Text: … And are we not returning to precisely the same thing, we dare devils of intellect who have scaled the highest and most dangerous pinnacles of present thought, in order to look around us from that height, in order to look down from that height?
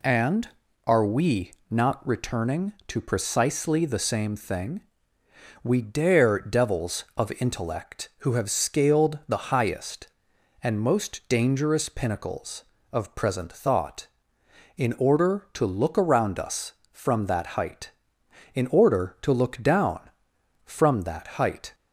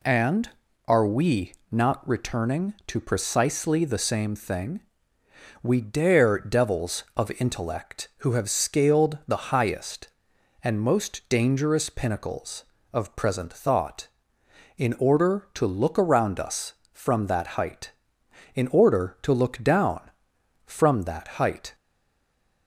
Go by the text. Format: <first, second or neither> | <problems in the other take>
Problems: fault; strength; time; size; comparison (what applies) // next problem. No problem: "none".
first | pauses between "we" and "not"; slight; at 1.5 s; 0.18 s long; slight in the first // stays silent after the last word; slight; from 21.7 s on; 0.9 s long